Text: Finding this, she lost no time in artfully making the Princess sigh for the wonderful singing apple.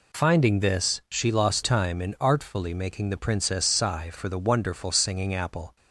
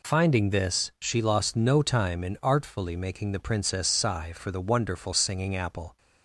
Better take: second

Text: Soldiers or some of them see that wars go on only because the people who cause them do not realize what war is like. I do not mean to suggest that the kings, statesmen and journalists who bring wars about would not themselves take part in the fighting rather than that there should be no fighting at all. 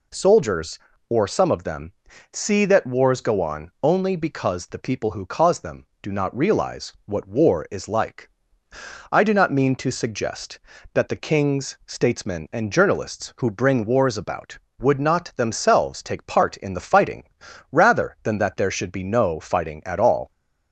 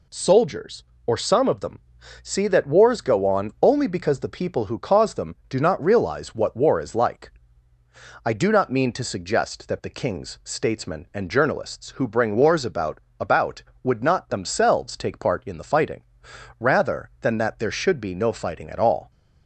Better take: first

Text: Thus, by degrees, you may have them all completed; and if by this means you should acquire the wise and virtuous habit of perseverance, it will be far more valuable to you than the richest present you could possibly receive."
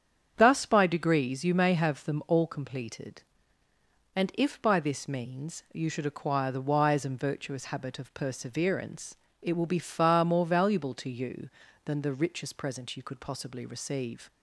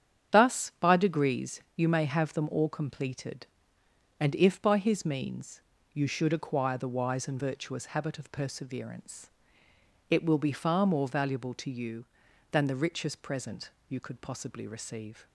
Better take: first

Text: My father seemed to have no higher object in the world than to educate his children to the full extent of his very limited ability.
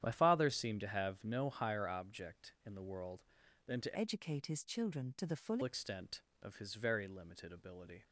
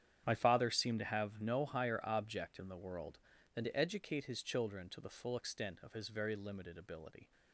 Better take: second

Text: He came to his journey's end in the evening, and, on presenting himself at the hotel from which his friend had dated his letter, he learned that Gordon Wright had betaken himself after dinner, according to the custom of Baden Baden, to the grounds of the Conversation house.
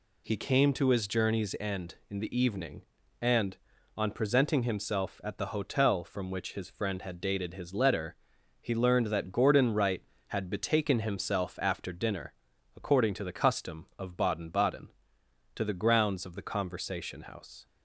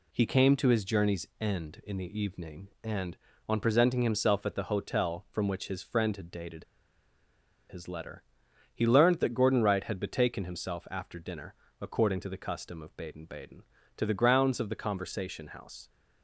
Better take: first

